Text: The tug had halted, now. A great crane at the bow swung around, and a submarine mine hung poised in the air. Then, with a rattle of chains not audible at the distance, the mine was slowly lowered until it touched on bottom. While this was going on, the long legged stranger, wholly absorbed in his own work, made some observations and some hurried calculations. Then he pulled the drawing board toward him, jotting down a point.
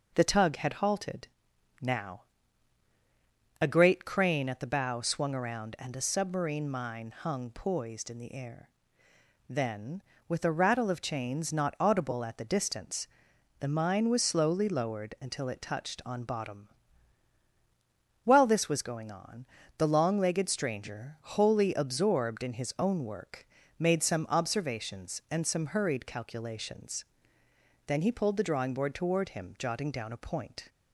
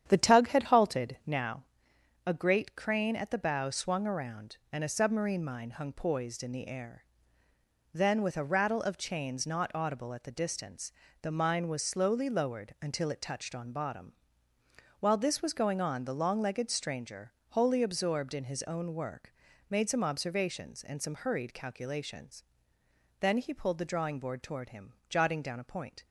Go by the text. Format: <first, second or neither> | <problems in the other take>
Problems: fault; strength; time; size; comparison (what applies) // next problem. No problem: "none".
first | starts louder than the rest; strong; until 1.5 s; 9.5 dB